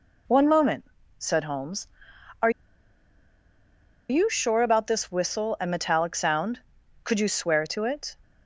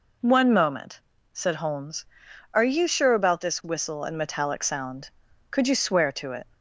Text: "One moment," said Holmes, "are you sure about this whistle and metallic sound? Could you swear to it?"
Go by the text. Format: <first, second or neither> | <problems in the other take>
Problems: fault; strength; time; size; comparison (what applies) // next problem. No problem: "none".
second | pauses between "are" and "you"; strong; at 2.4 s; 1.6 s long